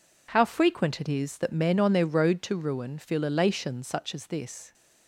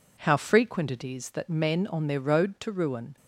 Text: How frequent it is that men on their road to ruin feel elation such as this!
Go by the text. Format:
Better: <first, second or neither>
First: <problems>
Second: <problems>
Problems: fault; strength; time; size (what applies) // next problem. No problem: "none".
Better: first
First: none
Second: stops before "feel elation such as this"; at 3.1 s